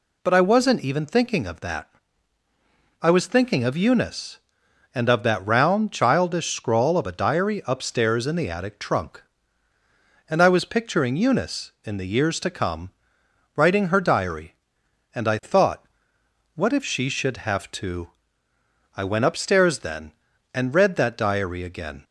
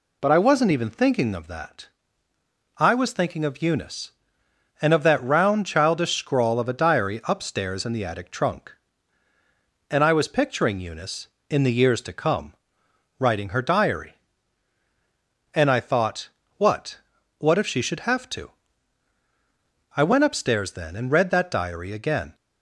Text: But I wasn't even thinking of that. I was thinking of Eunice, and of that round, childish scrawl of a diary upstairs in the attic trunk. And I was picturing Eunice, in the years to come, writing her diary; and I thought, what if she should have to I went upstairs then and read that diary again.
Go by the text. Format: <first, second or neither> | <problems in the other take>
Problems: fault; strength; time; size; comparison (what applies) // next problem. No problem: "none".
first | says "what" twice; at 17.3 s // pauses between "to" and "I"; strong; at 18.5 s; 1.4 s long; noticeable in the first